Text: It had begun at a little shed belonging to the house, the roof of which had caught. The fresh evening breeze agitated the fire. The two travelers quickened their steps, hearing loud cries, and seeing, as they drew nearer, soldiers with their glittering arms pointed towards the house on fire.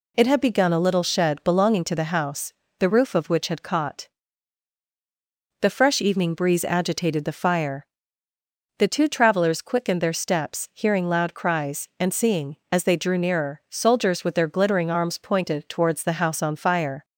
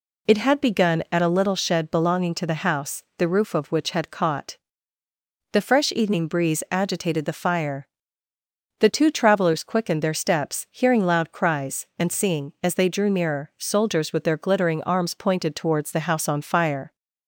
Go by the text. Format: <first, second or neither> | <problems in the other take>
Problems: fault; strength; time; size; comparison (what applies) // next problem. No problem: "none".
second | skips "at"; at 0.7 s